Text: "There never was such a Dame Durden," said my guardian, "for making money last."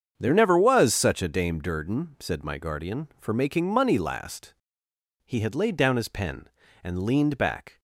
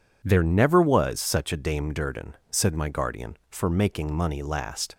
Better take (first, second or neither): second